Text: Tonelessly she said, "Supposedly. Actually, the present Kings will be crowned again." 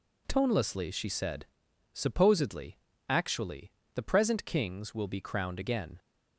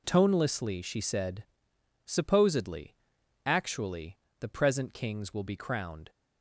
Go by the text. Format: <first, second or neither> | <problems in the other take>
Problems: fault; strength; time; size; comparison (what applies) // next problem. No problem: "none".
first | stops before "again"; at 6.0 s